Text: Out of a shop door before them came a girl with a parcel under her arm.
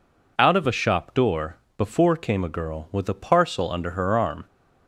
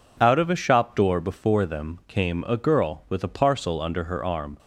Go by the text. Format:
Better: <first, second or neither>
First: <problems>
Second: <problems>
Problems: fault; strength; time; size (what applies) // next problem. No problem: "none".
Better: second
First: pauses between "door" and "before"; slight; at 1.5 s; 0.18 s long // skips "them"; at 2.1 s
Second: none